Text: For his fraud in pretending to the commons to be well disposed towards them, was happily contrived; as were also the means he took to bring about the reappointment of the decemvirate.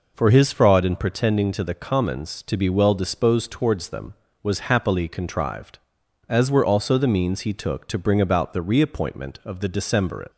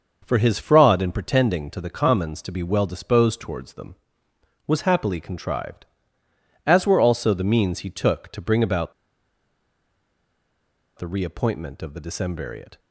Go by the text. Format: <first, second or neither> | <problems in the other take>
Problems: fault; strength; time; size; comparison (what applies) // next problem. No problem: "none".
first | starts louder than the rest; noticeable; until 1.2 s; 6 dB // pauses between "about" and "the"; strong; at 8.9 s; 2.0 s long